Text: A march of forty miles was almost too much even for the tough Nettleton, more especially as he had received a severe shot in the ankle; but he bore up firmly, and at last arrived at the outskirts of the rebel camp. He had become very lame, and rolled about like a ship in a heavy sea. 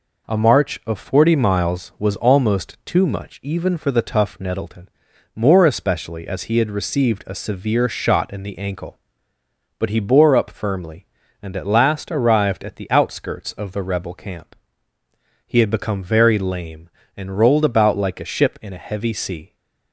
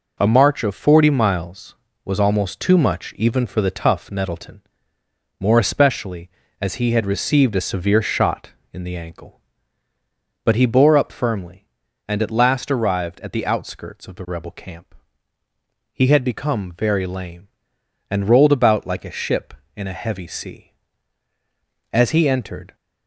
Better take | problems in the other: first | goes on to say "As he entered"; noticeable; from 21.9 s on; 0.82 s long

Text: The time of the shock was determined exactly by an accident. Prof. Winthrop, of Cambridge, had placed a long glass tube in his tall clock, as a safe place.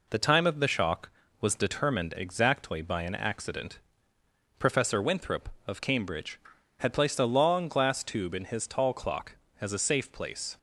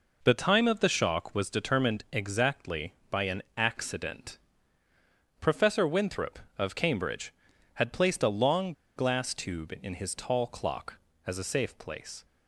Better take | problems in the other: first | pauses between "an" and "accident"; slight; at 3.4 s; 0.16 s long // pauses between "long" and "glass"; slight; at 8.7 s; 0.24 s long

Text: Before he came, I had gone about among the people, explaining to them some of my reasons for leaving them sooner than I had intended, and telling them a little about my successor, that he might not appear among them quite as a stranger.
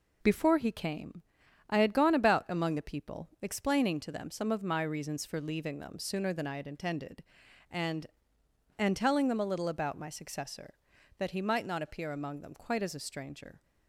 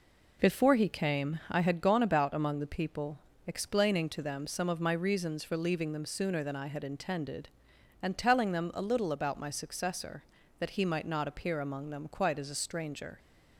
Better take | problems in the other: second | says "and" twice; at 8.7 s

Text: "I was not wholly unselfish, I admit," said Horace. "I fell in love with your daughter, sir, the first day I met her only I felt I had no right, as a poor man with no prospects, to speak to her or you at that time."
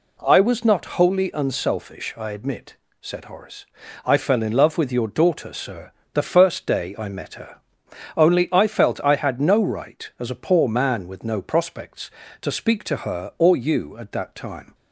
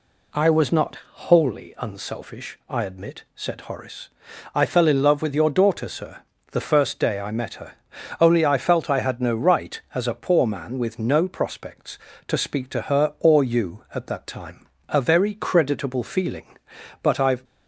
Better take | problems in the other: first | pauses between "not" and "wholly"; slight; at 0.9 s; 0.16 s long // pauses between "her" and "only"; noticeable; at 7.7 s; 0.48 s long; noticeable in the first // goes on to say "A very creditable feeling but I've"; strong; from 14.8 s on; 2.5 s long

